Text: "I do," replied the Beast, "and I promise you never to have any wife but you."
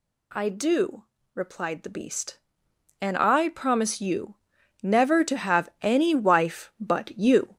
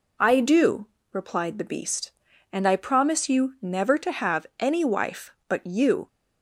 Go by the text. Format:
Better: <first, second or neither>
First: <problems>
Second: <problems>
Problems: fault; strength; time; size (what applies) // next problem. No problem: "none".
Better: second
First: gets louder; noticeable; throughout; 4.5 dB // pauses between "you" and "never"; noticeable; at 4.3 s; 0.46 s long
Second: none